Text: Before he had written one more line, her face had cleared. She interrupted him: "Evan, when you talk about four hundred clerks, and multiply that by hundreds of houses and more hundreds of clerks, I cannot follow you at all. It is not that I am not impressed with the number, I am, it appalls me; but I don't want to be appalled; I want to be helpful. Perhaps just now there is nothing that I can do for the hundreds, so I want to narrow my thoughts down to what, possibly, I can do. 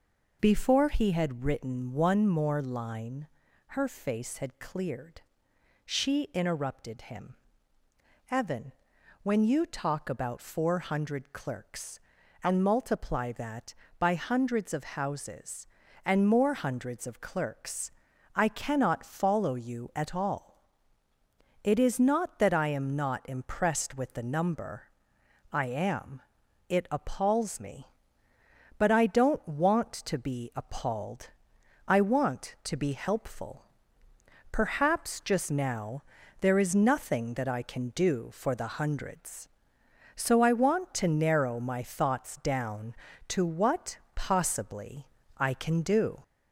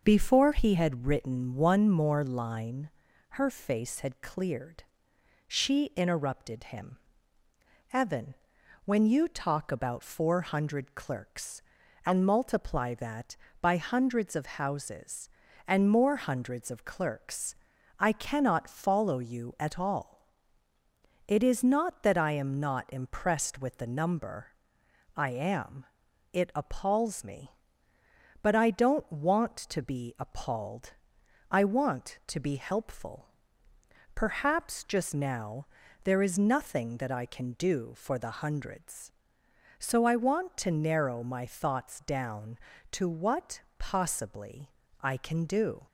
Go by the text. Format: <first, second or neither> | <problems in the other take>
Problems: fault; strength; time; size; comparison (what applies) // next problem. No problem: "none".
second | gets louder; slight; throughout; 2.5 dB // pauses between "now" and "there"; slight; at 36.0 s; 0.36 s long; slight in the second